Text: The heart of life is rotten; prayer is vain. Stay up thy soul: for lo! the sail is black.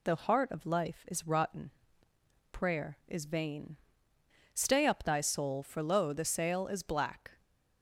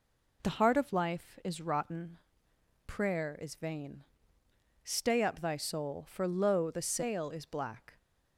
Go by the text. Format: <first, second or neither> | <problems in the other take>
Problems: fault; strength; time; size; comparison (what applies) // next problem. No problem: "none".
neither | none